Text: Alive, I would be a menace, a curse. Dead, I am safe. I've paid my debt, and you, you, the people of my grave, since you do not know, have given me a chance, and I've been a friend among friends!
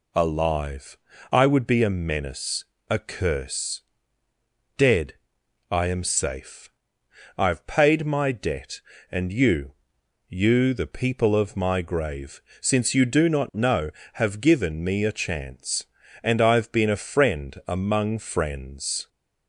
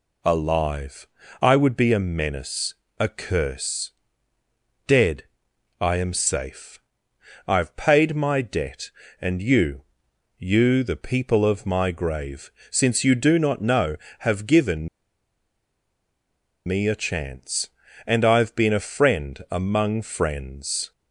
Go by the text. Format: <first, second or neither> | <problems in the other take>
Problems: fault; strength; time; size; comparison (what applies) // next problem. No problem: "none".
first | pauses between "given" and "me"; strong; at 14.8 s; 1.7 s long